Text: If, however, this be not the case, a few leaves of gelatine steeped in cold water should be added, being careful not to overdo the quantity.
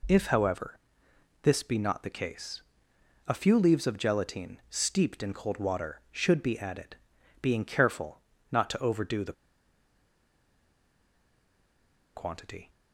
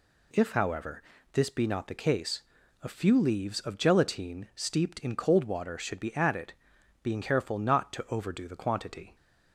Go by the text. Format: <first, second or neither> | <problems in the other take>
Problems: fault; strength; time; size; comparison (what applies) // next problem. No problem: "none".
second | pauses between "careful" and "not"; slight; at 8.2 s; 0.32 s long // pauses between "the" and "quantity"; strong; at 9.3 s; 2.8 s long